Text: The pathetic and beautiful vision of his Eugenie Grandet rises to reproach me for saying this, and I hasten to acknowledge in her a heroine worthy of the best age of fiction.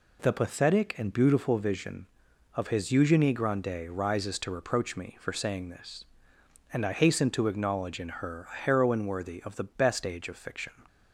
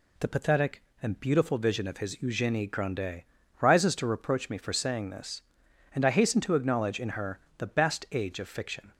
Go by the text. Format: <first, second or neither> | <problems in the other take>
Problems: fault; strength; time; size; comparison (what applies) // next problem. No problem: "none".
first | pauses between "Grandet" and "rises"; slight; at 3.2 s; 0.36 s long // skips "a heroine worthy of"; at 7.4 s